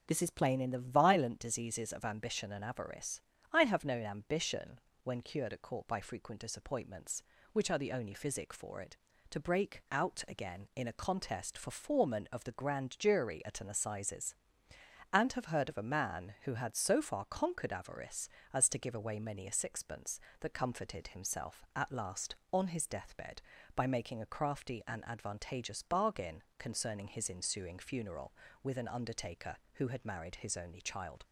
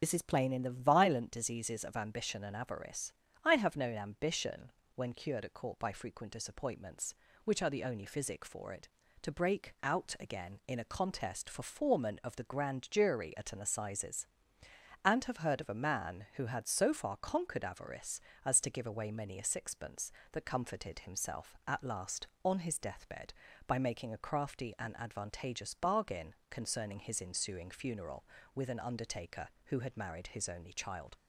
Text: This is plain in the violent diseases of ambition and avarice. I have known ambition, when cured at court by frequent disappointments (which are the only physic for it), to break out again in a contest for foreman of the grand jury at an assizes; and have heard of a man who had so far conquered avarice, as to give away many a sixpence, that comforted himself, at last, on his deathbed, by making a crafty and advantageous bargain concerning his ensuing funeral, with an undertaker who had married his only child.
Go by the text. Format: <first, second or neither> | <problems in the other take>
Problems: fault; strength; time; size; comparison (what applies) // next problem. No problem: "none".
first | loses the start of "This"; at 0.0 s; 30 ms // starts louder than the rest; strong; until 1.0 s; 7.5 dB; also in the first // pauses between "bargain" and "concerning"; slight; at 26.3 s; 0.16 s long; slight in the first